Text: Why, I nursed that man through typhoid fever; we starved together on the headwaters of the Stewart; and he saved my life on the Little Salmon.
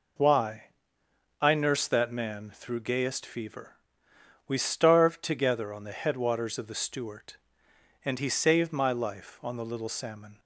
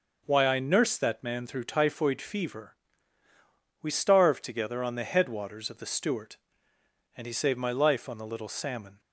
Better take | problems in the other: second | says "gayest" for "typhoid"; at 2.7 s

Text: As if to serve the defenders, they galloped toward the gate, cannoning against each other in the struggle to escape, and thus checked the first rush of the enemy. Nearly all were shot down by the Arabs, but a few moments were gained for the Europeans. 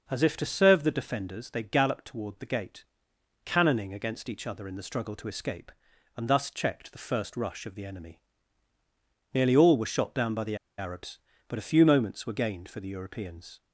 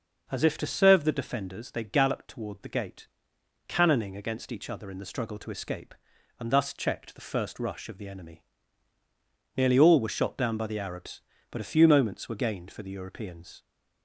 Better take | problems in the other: second | pauses between "the" and "Arabs"; slight; at 10.5 s; 0.21 s long

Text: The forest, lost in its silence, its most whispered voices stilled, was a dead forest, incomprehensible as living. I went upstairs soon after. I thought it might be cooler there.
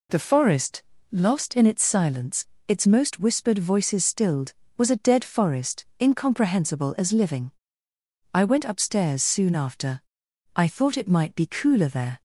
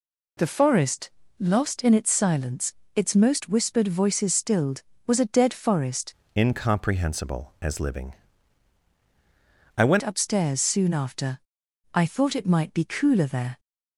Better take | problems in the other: first | changes voice from "incomprehensible" to "went"; from 6.3 to 9.9 s; 3.6 s long

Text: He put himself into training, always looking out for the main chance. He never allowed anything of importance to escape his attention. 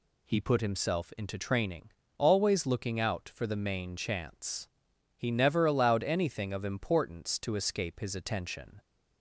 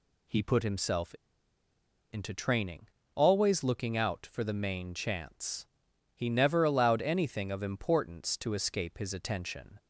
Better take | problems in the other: first | pauses between "himself" and "into"; noticeable; at 1.1 s; 0.97 s long

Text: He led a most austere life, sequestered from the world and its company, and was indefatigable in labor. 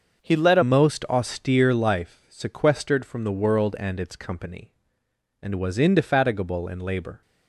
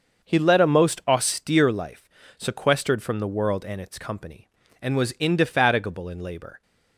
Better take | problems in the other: second | starts louder than the rest; until 1.2 s; 6.5 dB; also in the second // changes voice at "most"; from 0.6 s on; 6.6 s long

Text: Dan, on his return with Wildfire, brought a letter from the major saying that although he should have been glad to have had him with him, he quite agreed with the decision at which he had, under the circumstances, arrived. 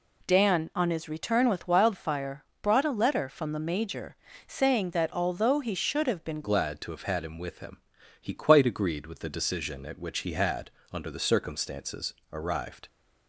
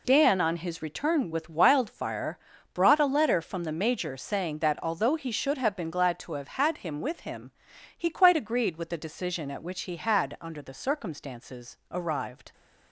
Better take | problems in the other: second | pauses between "major" and "saying"; slight; at 4.1 s; 0.32 s long // changes voice at "glad"; from 6.4 s on; 6.4 s long

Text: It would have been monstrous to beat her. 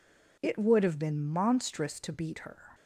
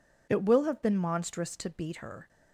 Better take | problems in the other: first | says "will" for "would"; at 0.4 s

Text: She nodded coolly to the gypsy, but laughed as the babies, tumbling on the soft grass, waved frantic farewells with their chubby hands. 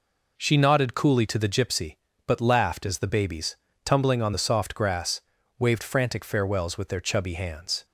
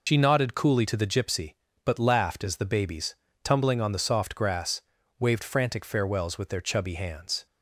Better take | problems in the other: first | loses the start of "She"; at 0.0 s; 90 ms

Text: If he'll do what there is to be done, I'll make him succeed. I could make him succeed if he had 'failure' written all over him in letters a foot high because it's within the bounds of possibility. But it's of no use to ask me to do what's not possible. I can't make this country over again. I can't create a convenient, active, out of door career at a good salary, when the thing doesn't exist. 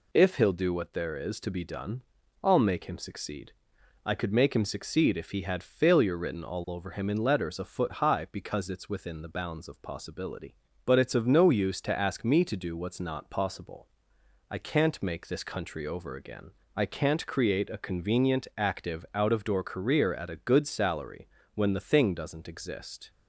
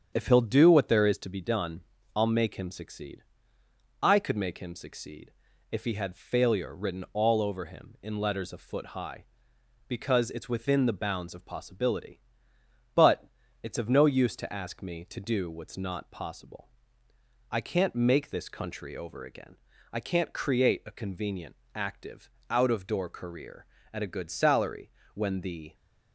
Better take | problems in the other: first | starts louder than the rest; strong; until 1.1 s; 8 dB // pauses between "succeed" and "if"; at 5.3 s; 0.38 s long // pauses between "But" and "it's"; slight; at 13.2 s; 0.36 s long // stops before "thing doesn't exist"; at 25.7 s

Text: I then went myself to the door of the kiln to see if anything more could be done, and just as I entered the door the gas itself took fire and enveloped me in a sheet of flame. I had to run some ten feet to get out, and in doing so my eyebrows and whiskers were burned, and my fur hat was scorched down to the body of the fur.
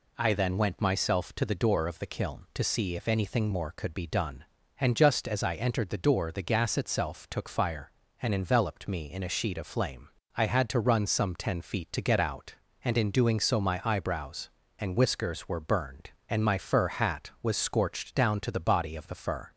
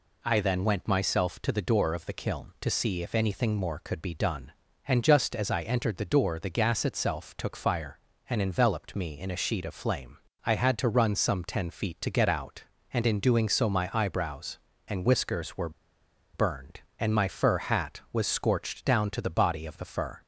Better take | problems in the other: first | pauses between "were" and "burned"; noticeable; at 15.6 s; 0.64 s long

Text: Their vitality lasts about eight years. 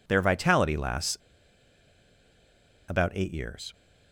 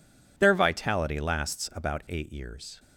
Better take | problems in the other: second | pauses between "lasts" and "about"; strong; at 1.1 s; 1.7 s long

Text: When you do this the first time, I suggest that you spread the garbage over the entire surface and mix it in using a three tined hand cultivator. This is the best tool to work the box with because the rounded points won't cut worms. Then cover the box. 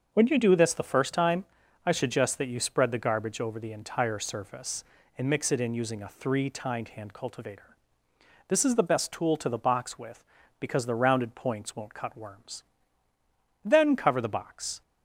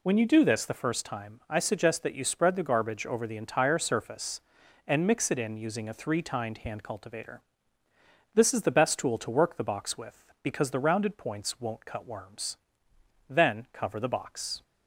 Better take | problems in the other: second | starts louder than the rest; until 1.1 s; 6.5 dB // skips "work"; at 9.4 s

